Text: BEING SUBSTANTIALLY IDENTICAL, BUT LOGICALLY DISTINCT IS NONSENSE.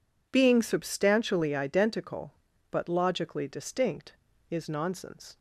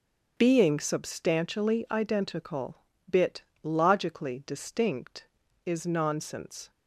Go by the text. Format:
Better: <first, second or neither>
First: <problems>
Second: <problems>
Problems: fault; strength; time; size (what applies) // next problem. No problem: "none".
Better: first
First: none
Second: starts louder than the rest; until 1.3 s; 7 dB // says "Bit" for "BUT"; at 3.0 s